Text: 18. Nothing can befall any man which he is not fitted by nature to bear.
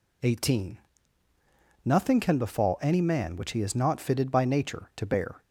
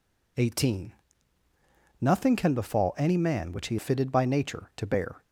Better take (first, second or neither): first